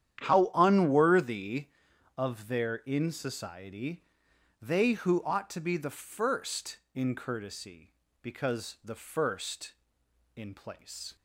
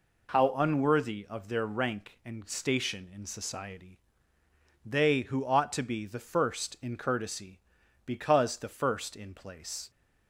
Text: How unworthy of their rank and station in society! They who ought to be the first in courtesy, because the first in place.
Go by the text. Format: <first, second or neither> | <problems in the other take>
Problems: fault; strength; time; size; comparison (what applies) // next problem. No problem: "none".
second | starts louder than the rest; strong; until 1.2 s; 10 dB // skips "rank and station"; at 2.8 s